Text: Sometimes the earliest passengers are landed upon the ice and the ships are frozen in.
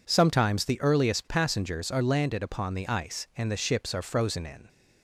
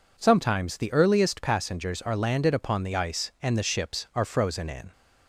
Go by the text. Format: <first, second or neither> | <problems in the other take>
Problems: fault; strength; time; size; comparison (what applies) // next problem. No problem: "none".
neither | none